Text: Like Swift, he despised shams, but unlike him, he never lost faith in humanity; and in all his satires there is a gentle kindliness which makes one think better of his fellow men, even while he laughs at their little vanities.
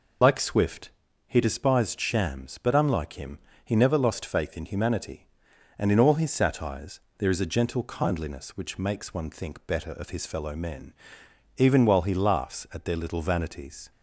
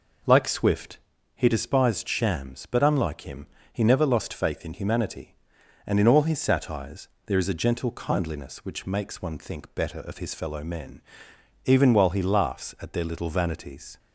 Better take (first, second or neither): second